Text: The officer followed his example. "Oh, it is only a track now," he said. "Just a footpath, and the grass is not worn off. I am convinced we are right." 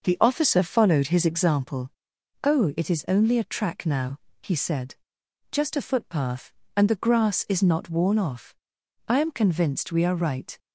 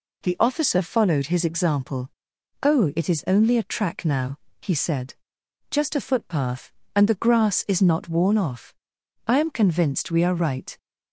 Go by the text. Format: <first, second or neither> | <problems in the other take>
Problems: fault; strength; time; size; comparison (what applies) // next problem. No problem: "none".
second | starts louder than the rest; noticeable; until 1.7 s; 6 dB